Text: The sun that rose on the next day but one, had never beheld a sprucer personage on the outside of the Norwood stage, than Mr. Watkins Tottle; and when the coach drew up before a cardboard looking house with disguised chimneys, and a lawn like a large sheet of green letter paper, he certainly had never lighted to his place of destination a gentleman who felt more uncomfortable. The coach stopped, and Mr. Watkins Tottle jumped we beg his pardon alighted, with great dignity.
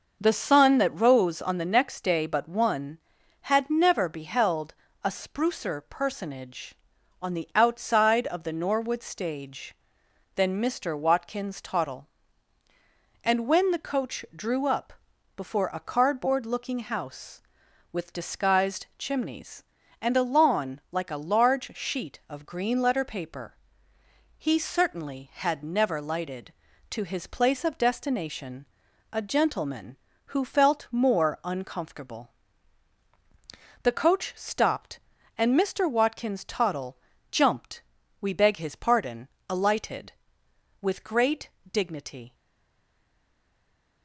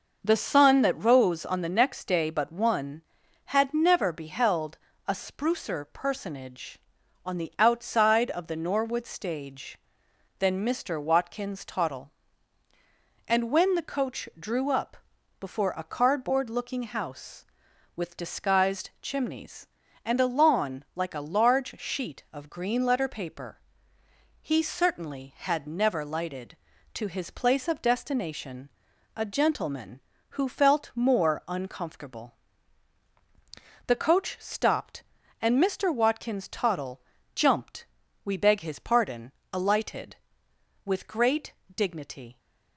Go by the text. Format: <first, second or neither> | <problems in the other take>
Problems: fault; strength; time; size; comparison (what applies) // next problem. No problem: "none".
second | pauses between "beheld" and "a"; slight; at 4.7 s; 0.30 s long; slight in the second // pauses between "up" and "before"; at 14.9 s; 0.44 s long; also in the second // pauses between "destination" and "a"; noticeable; at 28.6 s; 0.46 s long; noticeable in the second // pauses between "Tottle" and "jumped"; slight; at 36.9 s; 0.32 s long; slight in the second // pauses between "jumped" and "we"; at 37.8 s; 0.40 s long; also in the second // pauses between "pardon" and "alighted"; slight; at 39.2 s; 0.22 s long; slight in the second // pauses between "great" and "dignity"; slight; at 41.4 s; 0.22 s long; slight in the second // stays silent after the last word; noticeable; from 42.3 s on; 1.7 s long